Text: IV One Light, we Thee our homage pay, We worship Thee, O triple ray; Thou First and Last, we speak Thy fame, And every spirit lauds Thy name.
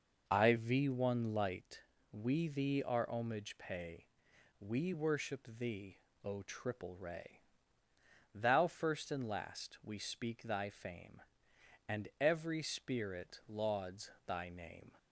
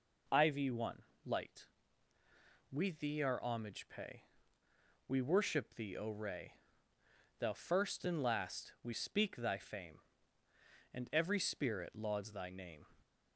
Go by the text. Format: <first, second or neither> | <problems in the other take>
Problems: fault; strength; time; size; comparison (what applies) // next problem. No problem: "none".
first | pauses between "One" and "Light"; slight; at 1.0 s; 0.22 s long // skips "triple"; at 6.0 s